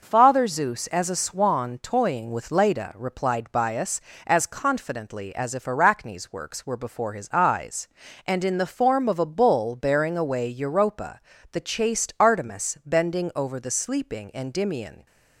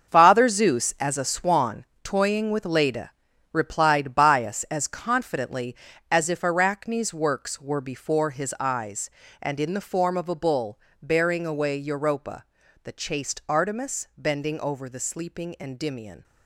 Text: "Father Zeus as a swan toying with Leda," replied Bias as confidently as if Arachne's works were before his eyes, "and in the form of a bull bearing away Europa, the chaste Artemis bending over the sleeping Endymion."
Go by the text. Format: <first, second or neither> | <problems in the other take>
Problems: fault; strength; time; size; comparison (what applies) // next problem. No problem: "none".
first | gets quieter; strong; throughout; 11 dB // pauses between "swan" and "toying"; slight; at 1.8 s; 0.16 s long // pauses between "bull" and "bearing"; slight; at 10.7 s; 0.20 s long